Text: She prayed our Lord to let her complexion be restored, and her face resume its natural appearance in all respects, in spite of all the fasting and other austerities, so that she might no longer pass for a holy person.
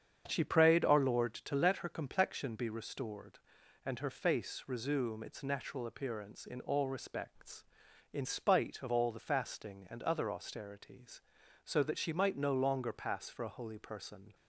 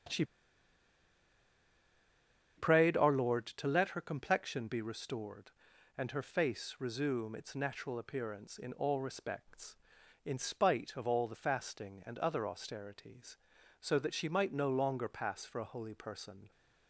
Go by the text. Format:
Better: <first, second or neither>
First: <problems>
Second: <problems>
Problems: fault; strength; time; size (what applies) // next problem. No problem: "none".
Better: first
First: starts louder than the rest; strong; until 1.2 s; 8 dB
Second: starts louder than the rest; strong; until 3.4 s; 8 dB // pauses between "She" and "prayed"; strong; at 0.2 s; 2.3 s long